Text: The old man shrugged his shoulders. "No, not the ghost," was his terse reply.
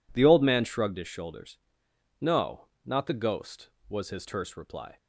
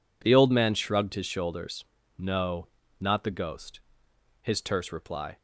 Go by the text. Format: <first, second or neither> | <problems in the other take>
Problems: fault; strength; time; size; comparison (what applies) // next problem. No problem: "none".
first | skips "was"; at 4.0 s